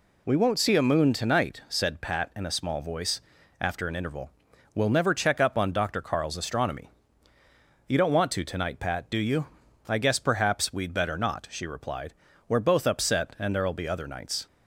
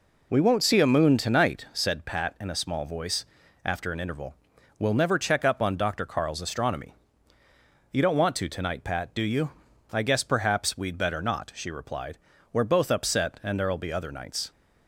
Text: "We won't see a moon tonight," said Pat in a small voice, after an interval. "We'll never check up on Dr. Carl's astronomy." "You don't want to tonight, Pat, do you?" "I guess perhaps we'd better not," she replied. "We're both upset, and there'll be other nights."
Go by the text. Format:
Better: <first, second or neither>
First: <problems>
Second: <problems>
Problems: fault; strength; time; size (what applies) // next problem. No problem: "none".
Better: first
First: none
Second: starts louder than the rest; until 1.9 s; 3.5 dB